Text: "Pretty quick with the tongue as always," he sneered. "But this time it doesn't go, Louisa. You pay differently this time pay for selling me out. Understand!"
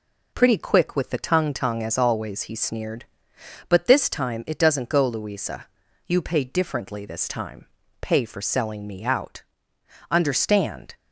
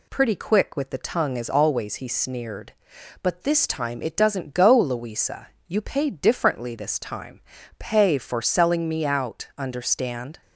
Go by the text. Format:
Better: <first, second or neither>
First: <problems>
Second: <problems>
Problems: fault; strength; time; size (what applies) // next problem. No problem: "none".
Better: second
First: says "tongue" twice; at 1.5 s // pauses between "time" and "pay"; slight; at 7.6 s; 0.34 s long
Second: pauses between "time" and "pay"; at 7.4 s; 0.38 s long